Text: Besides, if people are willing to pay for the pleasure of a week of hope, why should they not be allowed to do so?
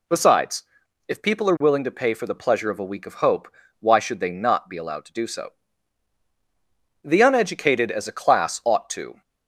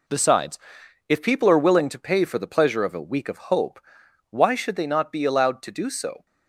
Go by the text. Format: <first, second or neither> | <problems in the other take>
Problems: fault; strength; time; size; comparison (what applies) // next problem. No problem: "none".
second | goes on to say "The uneducated as a class ought to"; strong; from 7.0 s on; 2.1 s long